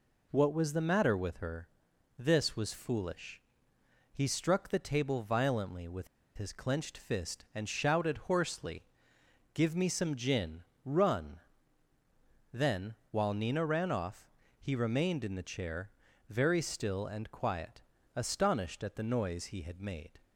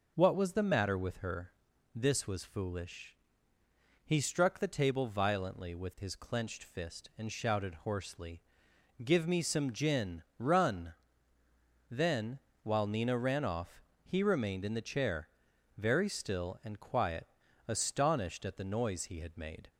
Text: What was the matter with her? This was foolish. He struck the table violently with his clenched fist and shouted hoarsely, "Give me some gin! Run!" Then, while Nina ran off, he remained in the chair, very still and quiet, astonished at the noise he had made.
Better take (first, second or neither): second